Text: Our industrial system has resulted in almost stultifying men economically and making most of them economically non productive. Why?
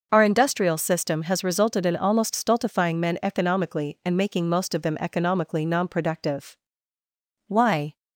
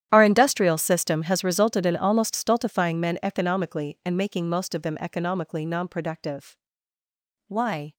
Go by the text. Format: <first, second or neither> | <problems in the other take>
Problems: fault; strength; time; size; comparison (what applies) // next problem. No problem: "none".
first | gets quieter; strong; throughout; 20 dB